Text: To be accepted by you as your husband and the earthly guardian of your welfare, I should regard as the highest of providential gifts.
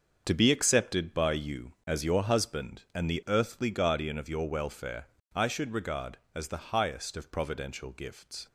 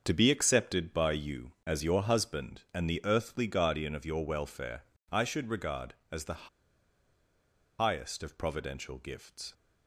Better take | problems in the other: first | starts louder than the rest; until 1.0 s; 6.5 dB; also in the first // pauses between "the" and "highest"; strong; at 6.4 s; 1.3 s long

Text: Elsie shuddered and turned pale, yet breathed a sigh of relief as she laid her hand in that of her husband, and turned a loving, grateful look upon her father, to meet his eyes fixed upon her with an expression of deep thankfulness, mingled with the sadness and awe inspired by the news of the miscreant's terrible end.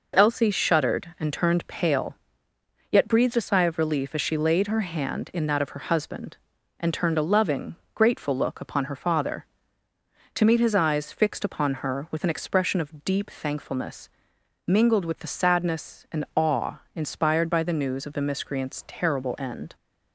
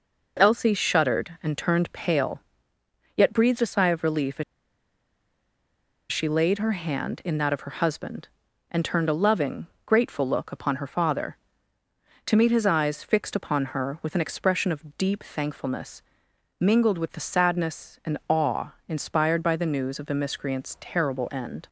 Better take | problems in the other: first | pauses between "as" and "she"; strong; at 4.4 s; 1.6 s long // pauses between "awe" and "inspired"; slight; at 18.7 s; 0.16 s long; slight in the first

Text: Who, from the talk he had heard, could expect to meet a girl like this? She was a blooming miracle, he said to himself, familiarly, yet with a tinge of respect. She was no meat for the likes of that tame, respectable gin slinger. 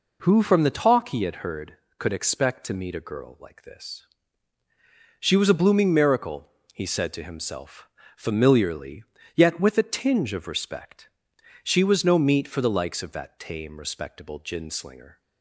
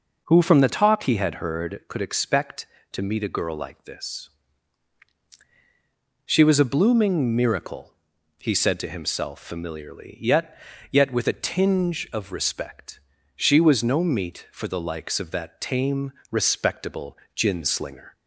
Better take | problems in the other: first | says "yet" twice; at 10.9 s // pauses between "respectable" and "gin"; slight; at 17.1 s; 0.18 s long

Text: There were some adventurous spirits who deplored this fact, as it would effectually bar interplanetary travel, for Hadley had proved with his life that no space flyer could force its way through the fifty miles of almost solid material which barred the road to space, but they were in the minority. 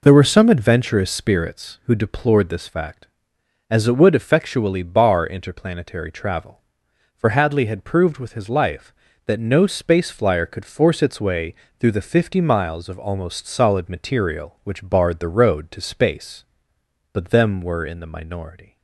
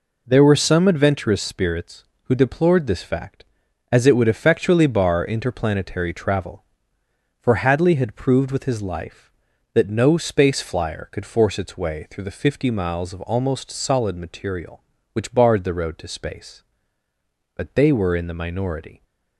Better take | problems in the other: second | pauses between "way" and "through"; slight; at 11.5 s; 0.26 s long // says "them" for "they"; at 17.2 s

